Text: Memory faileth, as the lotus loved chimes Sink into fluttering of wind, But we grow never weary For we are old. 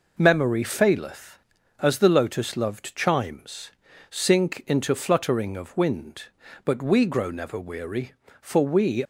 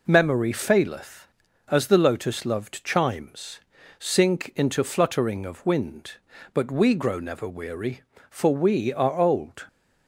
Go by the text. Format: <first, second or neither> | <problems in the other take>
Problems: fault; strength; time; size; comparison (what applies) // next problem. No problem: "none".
second | pauses between "chimes" and "Sink"; at 3.7 s; 0.38 s long; also in the second // stops before "are old"; at 9.0 s